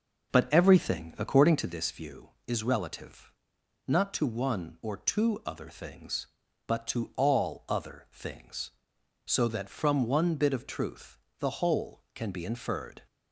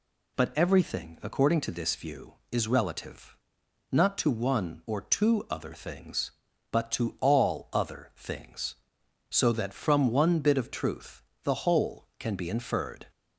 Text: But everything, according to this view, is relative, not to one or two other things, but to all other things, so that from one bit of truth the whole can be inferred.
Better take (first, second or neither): second